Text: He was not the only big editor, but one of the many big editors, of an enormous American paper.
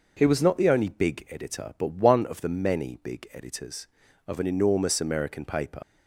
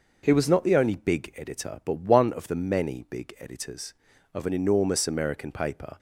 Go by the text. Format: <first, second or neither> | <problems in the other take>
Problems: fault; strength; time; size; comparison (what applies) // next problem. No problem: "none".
second | leaves "paper" unfinished; at 5.8 s; 90 ms